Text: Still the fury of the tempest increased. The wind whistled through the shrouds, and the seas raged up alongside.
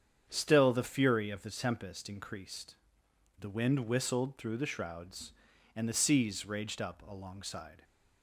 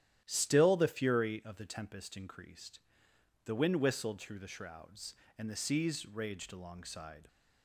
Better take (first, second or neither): first